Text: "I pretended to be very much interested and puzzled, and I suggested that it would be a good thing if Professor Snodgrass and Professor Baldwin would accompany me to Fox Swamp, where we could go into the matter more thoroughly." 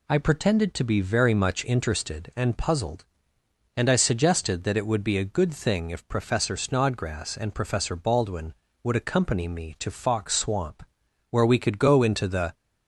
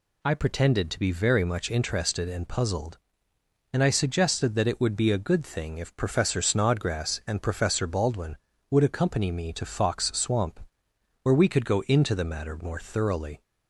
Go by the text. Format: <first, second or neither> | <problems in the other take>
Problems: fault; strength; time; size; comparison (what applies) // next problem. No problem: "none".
second | stops before "matter more thoroughly"; at 12.5 s